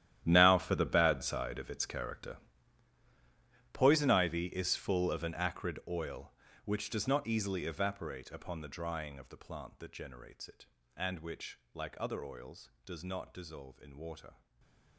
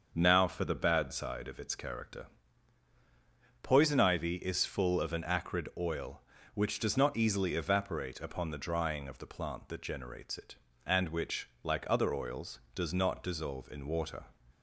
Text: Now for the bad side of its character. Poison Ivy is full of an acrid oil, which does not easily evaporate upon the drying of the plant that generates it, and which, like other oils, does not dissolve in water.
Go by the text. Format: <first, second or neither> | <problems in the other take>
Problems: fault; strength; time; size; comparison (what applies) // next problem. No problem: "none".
second | gets quieter; strong; throughout; 16.5 dB // starts louder than the rest; strong; until 1.2 s; 11.5 dB; also in the second // stays silent after the last word; slight; from 14.3 s on; 0.6 s long